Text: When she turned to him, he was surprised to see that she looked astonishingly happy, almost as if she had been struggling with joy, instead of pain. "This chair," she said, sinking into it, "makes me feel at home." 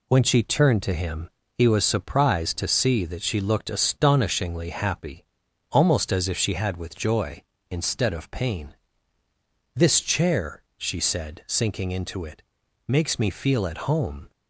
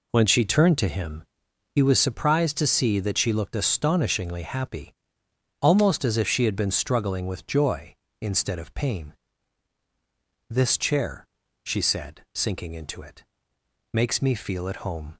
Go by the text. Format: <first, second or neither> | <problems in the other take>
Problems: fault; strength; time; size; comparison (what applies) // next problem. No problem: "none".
second | skips "been struggling"; at 6.7 s